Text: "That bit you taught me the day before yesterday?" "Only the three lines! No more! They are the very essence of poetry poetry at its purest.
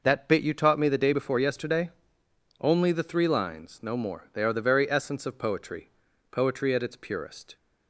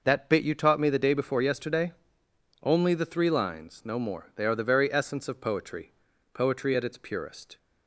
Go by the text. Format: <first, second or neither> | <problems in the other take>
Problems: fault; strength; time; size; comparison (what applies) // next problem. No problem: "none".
neither | pauses between "poetry" and "poetry"; the same in both